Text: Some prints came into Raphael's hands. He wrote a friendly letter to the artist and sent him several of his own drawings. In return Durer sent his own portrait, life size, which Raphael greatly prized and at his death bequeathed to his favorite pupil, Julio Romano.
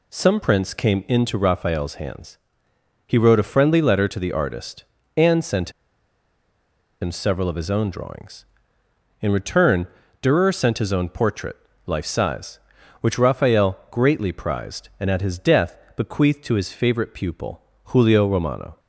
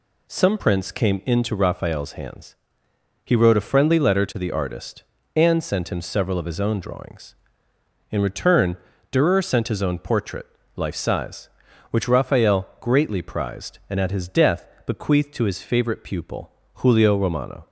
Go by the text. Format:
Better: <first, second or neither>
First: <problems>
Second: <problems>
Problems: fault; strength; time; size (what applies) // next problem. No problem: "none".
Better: second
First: pauses between "sent" and "him"; strong; at 5.7 s; 1.2 s long // pauses between "return" and "Durer"; slight; at 9.8 s; 0.34 s long // pauses between "death" and "bequeathed"; slight; at 15.7 s; 0.18 s long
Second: pauses between "return" and "Durer"; slight; at 8.7 s; 0.34 s long // pauses between "death" and "bequeathed"; slight; at 14.6 s; 0.18 s long